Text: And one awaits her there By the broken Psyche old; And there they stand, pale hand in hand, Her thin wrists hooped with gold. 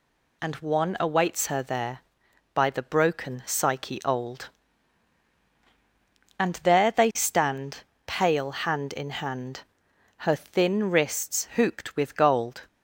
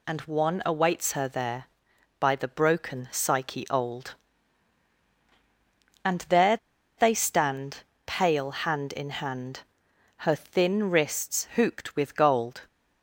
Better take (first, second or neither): first